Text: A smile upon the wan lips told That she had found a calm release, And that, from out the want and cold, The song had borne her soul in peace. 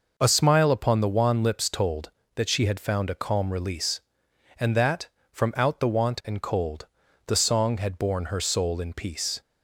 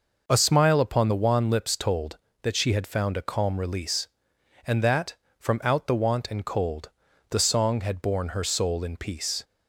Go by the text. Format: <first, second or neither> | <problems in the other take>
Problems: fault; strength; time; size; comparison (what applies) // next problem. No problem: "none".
neither | none